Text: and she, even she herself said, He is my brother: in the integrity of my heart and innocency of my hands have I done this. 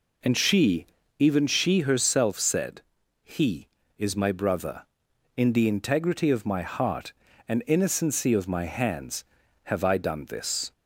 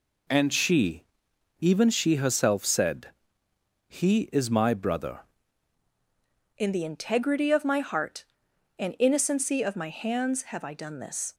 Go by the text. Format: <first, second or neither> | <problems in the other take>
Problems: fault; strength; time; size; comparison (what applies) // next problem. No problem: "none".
first | changes voice at "in"; from 6.5 s on; 4.8 s long